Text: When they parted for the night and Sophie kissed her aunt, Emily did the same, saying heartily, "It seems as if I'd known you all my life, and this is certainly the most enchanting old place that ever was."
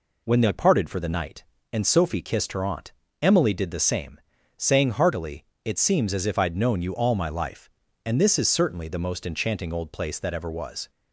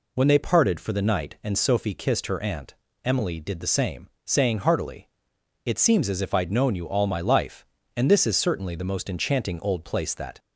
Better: first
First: none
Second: stops before "ever was"; at 10.3 s

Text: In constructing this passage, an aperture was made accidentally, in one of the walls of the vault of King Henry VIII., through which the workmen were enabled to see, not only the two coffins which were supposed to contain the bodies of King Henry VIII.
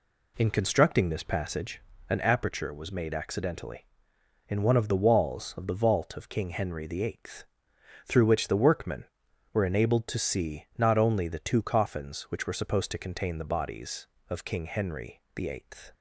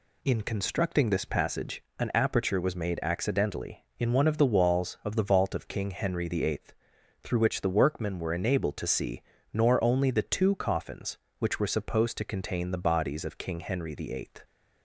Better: first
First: none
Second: says "nor" for "not"; at 9.5 s

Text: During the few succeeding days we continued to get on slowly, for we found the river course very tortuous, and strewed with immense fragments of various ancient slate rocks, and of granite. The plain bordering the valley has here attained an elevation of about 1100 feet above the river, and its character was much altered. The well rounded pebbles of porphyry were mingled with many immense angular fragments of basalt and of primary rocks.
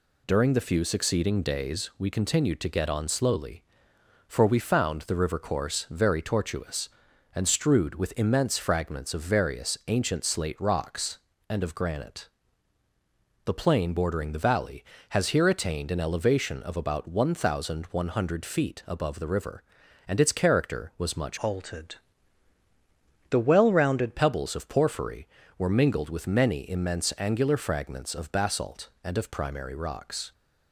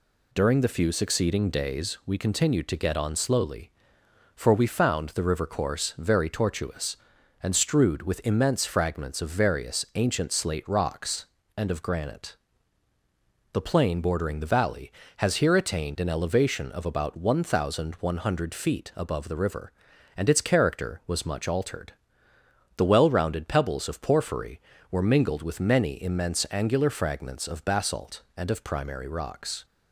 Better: second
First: changes voice from "altered" to "rounded"; from 21.4 to 24.1 s; 2.7 s long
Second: none

